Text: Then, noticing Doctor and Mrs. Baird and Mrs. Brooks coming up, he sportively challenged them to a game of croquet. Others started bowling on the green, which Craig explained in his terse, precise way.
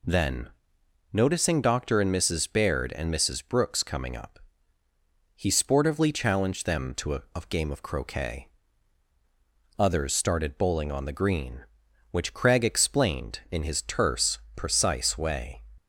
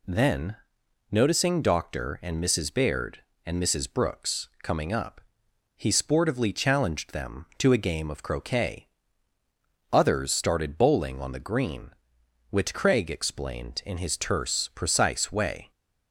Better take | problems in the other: second | says "a" twice; at 7.3 s

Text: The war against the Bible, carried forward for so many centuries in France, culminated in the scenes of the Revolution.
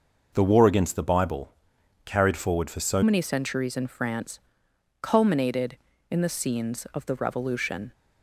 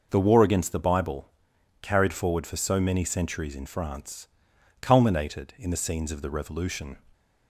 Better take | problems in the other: second | changes voice at "many"; from 3.0 s on; 4.9 s long

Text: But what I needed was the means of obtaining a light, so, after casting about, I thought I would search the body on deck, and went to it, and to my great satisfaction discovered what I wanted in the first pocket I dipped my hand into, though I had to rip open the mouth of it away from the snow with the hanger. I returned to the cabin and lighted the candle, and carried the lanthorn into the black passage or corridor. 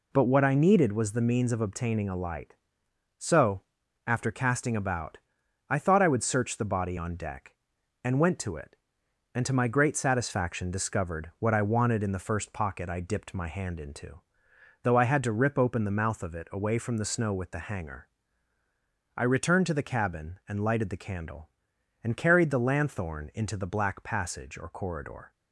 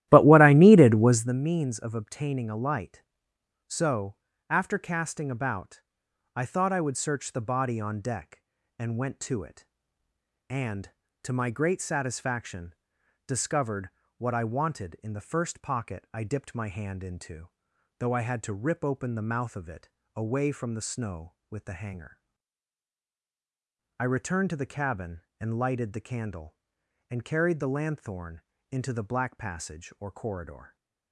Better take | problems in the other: first | starts louder than the rest; strong; until 1.4 s; 14 dB // pauses between "satisfaction" and "discovered"; noticeable; at 12.7 s; 0.52 s long // pauses between "discovered" and "what"; slight; at 13.8 s; 0.26 s long // pauses between "it" and "away"; slight; at 19.8 s; 0.26 s long // pauses between "lanthorn" and "into"; slight; at 28.3 s; 0.32 s long

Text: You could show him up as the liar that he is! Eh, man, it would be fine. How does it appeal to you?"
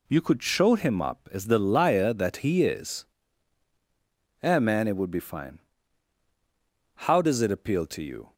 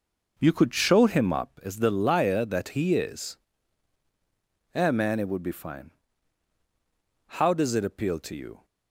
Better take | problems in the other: first | starts louder than the rest; noticeable; until 1.5 s; 5.5 dB

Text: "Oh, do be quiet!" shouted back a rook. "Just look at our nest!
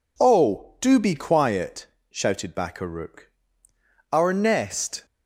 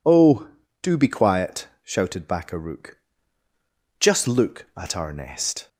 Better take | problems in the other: second | skips "Just look at"; at 3.7 s

